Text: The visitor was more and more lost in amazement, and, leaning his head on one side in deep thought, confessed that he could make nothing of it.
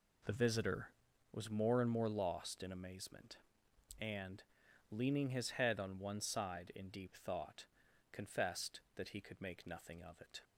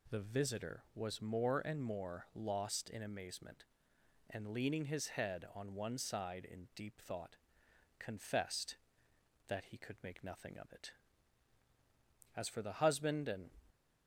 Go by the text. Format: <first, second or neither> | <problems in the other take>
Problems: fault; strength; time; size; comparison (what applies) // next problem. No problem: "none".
first | goes on to say "As for the husband and"; noticeable; from 12.3 s on; 1.2 s long